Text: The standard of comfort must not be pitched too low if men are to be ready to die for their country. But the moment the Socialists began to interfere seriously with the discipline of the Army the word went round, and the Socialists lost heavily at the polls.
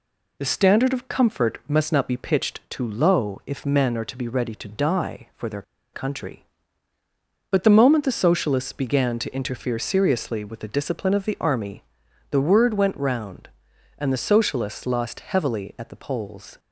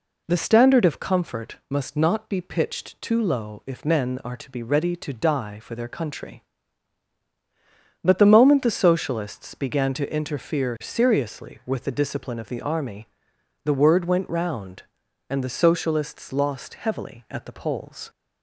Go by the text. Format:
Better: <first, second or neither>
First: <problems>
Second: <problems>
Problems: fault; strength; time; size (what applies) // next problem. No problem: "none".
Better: second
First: pauses between "their" and "country"; slight; at 5.6 s; 0.31 s long // pauses between "Army" and "the"; noticeable; at 11.8 s; 0.48 s long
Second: pauses between "Army" and "the"; noticeable; at 13.0 s; 0.56 s long